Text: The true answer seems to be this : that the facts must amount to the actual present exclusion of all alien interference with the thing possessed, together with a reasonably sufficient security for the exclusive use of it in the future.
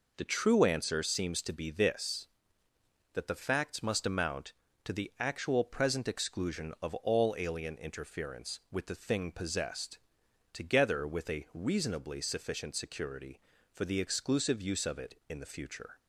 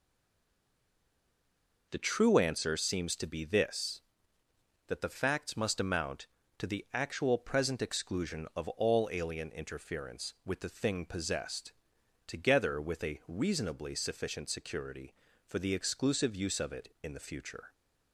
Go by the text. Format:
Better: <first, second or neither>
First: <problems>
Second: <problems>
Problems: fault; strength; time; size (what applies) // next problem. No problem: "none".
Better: first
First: none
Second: stays silent before the first word; noticeable; until 1.9 s; 1.9 s long